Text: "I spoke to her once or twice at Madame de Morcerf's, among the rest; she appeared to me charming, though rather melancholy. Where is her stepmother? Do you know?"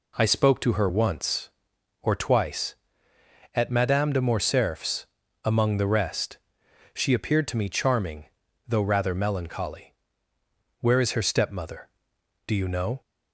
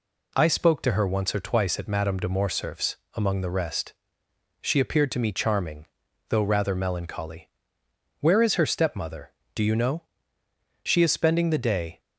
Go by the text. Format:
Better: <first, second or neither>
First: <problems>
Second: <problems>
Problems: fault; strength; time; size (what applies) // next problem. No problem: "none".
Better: first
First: none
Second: goes on to say "She is spending the day"; noticeable; from 10.8 s on; 1.1 s long